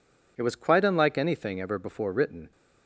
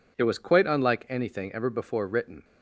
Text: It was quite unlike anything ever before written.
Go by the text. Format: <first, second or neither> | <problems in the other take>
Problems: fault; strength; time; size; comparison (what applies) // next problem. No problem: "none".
neither | none